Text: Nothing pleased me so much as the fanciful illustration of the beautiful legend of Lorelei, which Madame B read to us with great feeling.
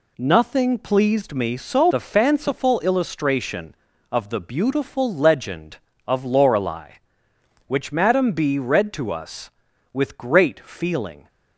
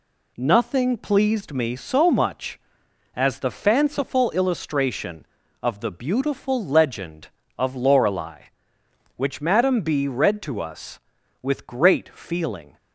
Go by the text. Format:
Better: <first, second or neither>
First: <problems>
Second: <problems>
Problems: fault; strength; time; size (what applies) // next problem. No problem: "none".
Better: second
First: skips "much as"; at 1.9 s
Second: none